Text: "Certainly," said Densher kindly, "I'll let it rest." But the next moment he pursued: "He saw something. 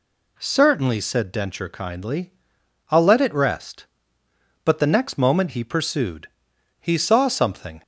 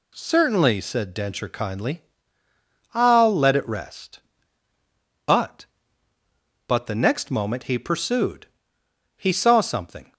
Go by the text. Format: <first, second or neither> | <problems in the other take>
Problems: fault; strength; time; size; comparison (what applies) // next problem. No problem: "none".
first | says "But" twice; at 6.6 s